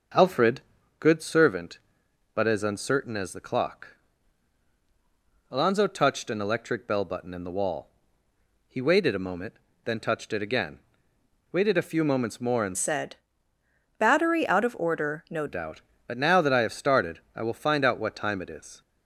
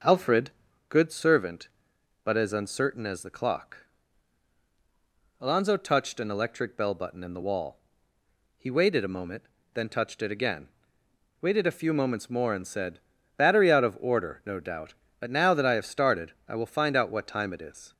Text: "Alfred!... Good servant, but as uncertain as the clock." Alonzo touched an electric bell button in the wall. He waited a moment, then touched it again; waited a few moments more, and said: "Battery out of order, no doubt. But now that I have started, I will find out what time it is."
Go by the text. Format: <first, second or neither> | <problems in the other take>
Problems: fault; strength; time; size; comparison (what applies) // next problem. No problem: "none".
second | starts louder than the rest; noticeable; until 1.5 s; 6 dB; noticeable in the second // changes voice from "said" to "no"; from 12.7 to 15.4 s; 2.7 s long